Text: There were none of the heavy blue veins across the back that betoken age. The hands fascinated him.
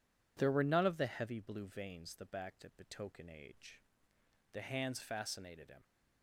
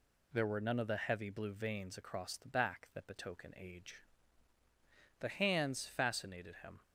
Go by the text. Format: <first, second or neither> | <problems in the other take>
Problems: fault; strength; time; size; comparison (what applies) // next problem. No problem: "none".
second | skips "across"; at 2.1 s